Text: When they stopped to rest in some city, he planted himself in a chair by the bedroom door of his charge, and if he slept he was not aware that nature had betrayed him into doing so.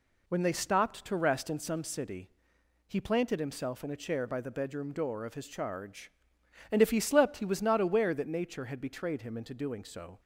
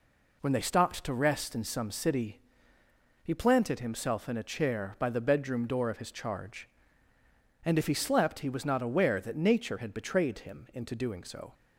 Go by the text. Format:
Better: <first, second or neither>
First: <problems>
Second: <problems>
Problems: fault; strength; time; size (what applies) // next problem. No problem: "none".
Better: neither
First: none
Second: none